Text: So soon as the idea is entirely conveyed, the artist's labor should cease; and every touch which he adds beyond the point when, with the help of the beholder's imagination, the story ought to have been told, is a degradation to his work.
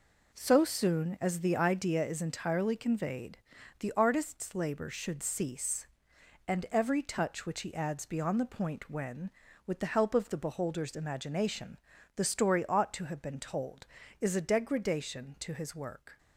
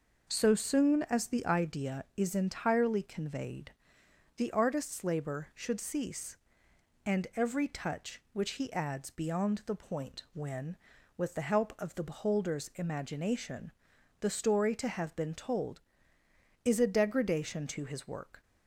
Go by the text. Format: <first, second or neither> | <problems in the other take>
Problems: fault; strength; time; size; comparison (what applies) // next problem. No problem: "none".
first | skips "ought"; at 14.7 s